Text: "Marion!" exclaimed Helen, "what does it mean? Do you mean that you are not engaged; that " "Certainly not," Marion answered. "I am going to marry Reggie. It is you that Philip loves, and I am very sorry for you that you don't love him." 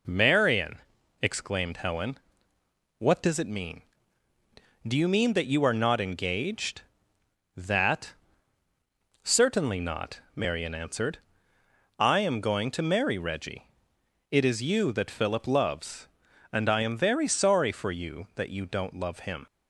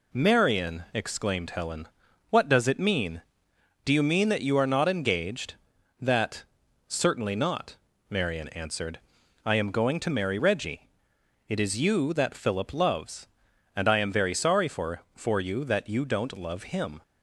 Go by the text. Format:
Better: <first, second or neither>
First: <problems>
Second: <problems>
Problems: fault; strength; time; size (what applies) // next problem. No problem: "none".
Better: first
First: none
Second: says "for" twice; at 15.1 s